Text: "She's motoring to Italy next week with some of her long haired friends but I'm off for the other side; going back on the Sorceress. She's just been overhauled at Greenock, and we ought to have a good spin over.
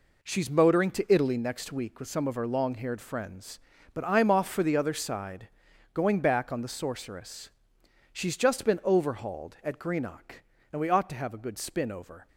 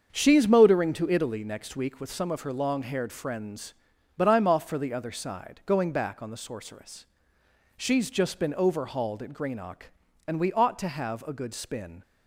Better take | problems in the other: first | starts louder than the rest; until 1.1 s; 7 dB // stops before "over"; at 12.0 s

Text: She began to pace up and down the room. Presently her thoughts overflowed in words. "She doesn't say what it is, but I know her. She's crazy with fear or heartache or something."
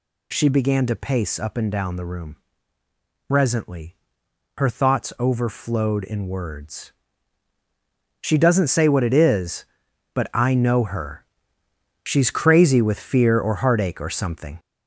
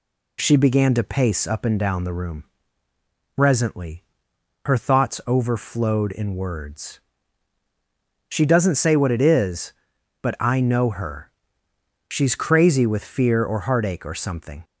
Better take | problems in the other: second | gets louder; noticeable; throughout; 5.5 dB // pauses between "Presently" and "her"; noticeable; at 3.9 s; 0.62 s long; noticeable in the second

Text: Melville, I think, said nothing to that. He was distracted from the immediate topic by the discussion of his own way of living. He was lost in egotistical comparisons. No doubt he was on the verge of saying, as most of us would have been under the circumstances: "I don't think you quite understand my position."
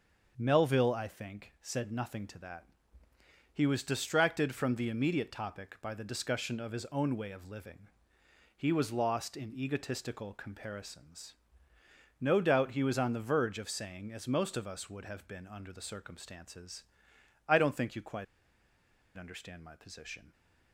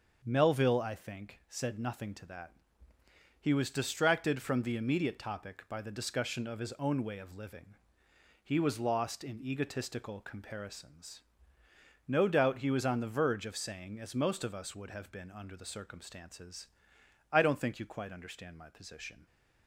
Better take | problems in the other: second | starts louder than the rest; until 1.3 s; 6.5 dB; also in the second // pauses between "quite" and "understand"; noticeable; at 18.2 s; 0.92 s long

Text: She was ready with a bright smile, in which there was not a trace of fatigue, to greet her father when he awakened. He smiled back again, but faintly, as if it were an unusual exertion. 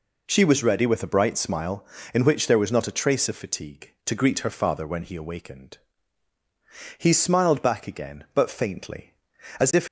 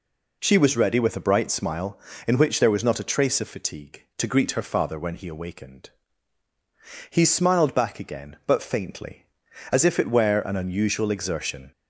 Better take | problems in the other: second | stops before "it were an unusual exertion"; at 9.8 s

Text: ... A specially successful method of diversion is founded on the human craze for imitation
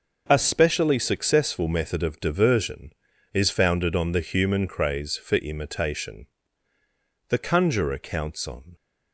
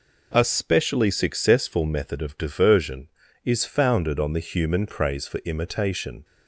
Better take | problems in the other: second | goes on to say "The conjurer counts on"; from 7.2 s on; 1.4 s long

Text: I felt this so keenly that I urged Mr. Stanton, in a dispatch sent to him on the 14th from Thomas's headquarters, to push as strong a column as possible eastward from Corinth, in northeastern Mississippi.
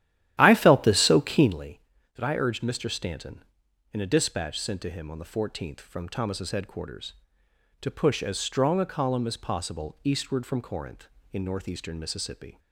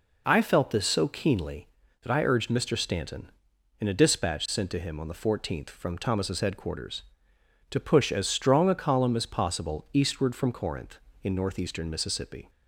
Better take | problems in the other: second | starts louder than the rest; strong; until 1.5 s; 12.5 dB

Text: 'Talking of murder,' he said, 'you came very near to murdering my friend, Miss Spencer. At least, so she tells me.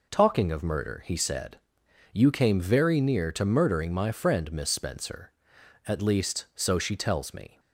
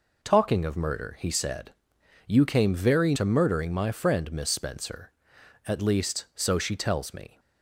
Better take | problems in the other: first | skips "near"; at 3.1 s

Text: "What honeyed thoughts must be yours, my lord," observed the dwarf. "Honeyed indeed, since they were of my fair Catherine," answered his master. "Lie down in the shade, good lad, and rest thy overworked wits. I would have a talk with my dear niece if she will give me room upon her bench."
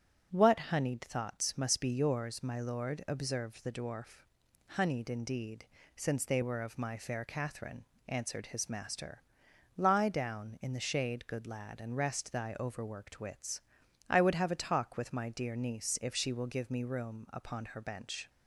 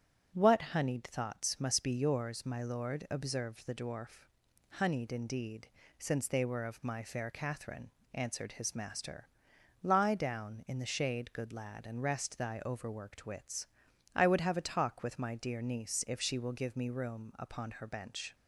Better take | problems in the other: neither | starts louder than the rest; strong; the same in both

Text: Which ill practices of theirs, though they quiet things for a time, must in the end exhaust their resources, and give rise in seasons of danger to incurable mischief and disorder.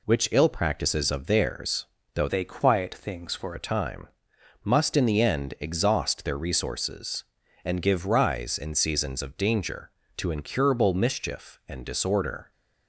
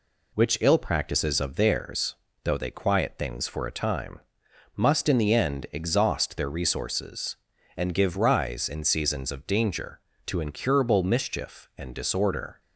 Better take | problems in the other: second | changes voice from "they" to "for"; from 2.2 to 3.5 s; 1.3 s long

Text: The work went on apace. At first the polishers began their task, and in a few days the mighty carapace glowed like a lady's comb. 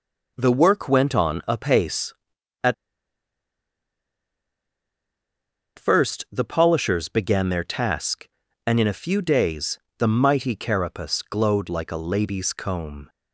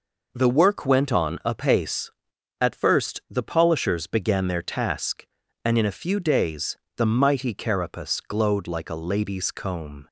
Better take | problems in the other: second | pauses between "At" and "first"; strong; at 2.7 s; 3.0 s long // pauses between "days" and "the"; slight; at 9.7 s; 0.22 s long; slight in the second

